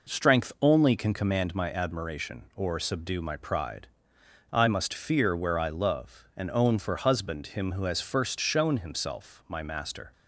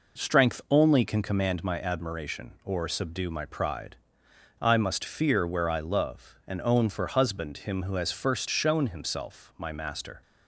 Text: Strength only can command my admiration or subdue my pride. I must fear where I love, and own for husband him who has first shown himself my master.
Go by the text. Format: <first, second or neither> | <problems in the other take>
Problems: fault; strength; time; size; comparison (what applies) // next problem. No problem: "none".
neither | none